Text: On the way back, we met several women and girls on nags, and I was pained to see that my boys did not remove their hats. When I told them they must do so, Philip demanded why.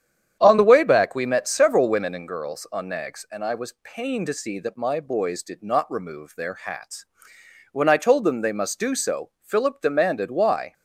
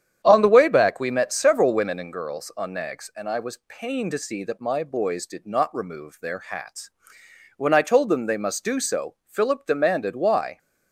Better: neither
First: starts louder than the rest; strong; until 1.4 s; 9 dB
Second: starts louder than the rest; strong; until 1.2 s; 9 dB

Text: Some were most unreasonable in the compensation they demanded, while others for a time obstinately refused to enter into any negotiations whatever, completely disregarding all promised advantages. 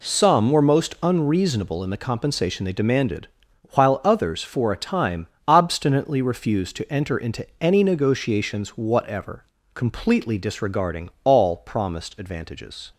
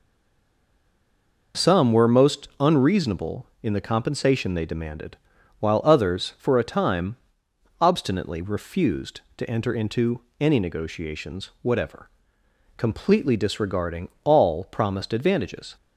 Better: first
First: pauses between "time" and "obstinately"; slight; at 5.2 s; 0.20 s long // pauses between "into" and "any"; slight; at 7.4 s; 0.16 s long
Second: stays silent before the first word; noticeable; until 1.5 s; 1.5 s long // pauses between "time" and "obstinately"; noticeable; at 7.1 s; 0.64 s long // pauses between "into" and "any"; slight; at 10.1 s; 0.18 s long

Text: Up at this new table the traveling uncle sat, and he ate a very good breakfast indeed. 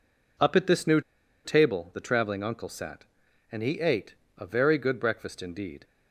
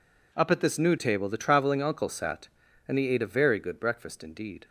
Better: second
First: pauses between "new" and "table"; at 0.9 s; 0.44 s long // pauses between "ate" and "a"; slight; at 4.1 s; 0.24 s long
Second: none

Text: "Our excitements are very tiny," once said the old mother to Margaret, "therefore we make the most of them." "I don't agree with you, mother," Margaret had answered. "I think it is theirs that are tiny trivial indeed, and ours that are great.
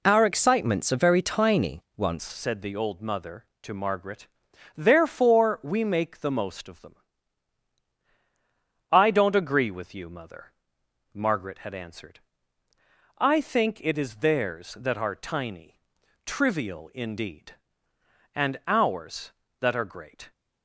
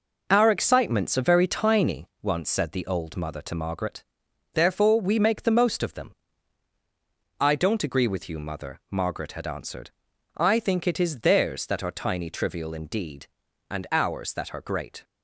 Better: second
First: changes voice at "said"; from 2.2 s on; 18.1 s long // pauses between "tiny" and "trivial"; noticeable; at 15.7 s; 0.46 s long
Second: none

